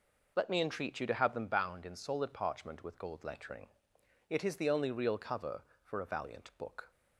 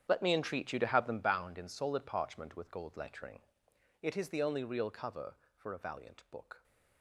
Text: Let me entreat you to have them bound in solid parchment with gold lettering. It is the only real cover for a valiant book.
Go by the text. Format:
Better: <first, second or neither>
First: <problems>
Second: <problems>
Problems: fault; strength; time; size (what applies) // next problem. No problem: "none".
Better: first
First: none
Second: gets quieter; strong; throughout; 15.5 dB